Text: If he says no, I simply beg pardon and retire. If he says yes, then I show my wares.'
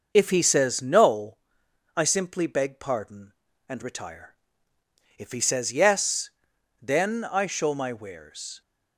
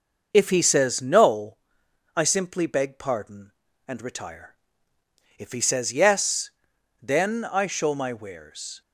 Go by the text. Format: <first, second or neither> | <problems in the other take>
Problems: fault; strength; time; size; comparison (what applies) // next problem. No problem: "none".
neither | none